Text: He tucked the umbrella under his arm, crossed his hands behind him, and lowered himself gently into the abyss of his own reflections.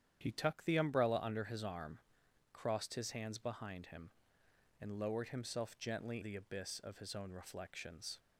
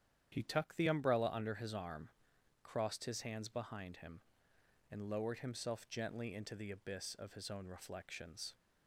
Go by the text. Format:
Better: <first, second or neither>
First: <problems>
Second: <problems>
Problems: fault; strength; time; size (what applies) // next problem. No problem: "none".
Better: second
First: starts louder than the rest; strong; until 1.2 s; 9.5 dB // skips "into"; at 6.2 s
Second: starts louder than the rest; strong; until 1.3 s; 9.5 dB